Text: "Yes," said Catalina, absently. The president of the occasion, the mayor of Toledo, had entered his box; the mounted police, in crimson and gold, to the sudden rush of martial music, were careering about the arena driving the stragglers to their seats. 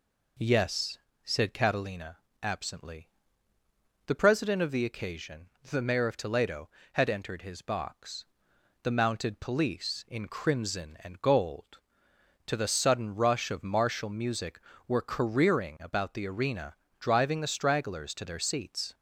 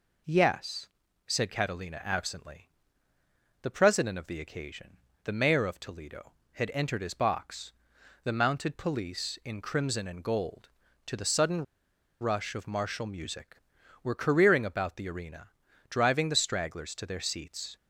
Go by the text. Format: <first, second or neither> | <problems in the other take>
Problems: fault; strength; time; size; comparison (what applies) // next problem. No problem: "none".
first | pauses between "sudden" and "rush"; noticeable; at 11.6 s; 0.58 s long // pauses between "arena" and "driving"; at 15.4 s; 0.40 s long; slight in the first